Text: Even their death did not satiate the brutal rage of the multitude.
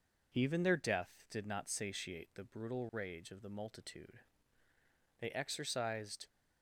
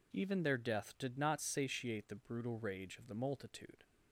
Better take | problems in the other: second | goes on to say "They exercised"; noticeable; from 5.2 s on; 1.0 s long

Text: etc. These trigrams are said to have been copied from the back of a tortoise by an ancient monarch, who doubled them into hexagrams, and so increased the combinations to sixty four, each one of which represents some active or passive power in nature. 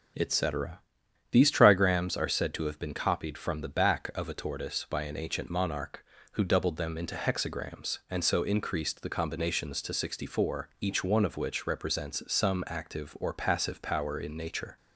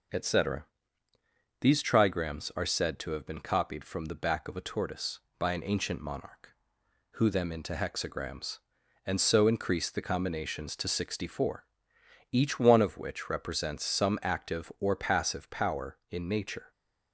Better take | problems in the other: first | starts louder than the rest; noticeable; until 2.0 s; 6 dB // skips "doubled"; at 7.2 s

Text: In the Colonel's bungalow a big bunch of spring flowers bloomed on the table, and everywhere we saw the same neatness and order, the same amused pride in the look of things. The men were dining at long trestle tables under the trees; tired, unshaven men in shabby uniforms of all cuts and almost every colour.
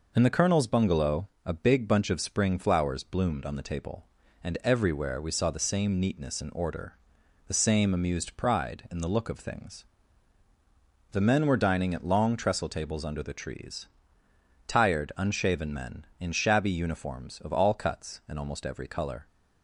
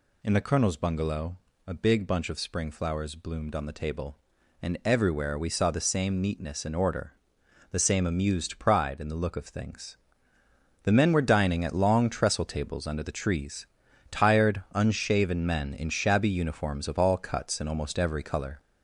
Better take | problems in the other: first | gets louder; throughout; 3.5 dB // pauses between "bungalow" and "a"; slight; at 1.3 s; 0.30 s long; slight in the first

